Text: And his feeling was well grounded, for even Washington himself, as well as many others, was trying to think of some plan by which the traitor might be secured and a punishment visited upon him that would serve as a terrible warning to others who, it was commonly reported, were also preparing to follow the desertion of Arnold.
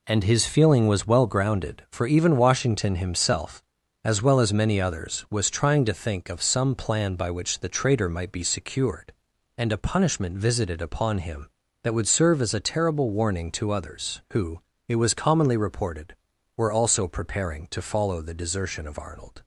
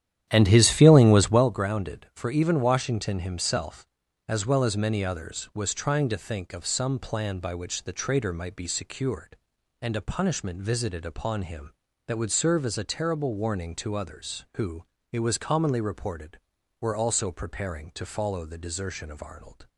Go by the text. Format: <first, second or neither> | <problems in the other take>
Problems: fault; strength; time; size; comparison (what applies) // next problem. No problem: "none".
first | starts louder than the rest; strong; until 1.4 s; 11 dB